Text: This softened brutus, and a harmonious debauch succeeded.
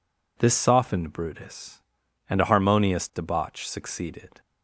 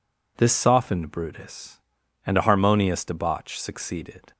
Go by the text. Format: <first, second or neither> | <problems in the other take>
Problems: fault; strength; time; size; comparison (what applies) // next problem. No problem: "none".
neither | none